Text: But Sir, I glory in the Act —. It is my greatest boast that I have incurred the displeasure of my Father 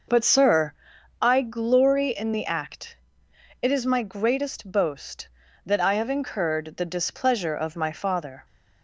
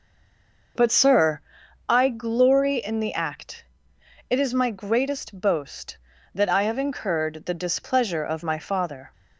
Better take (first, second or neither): first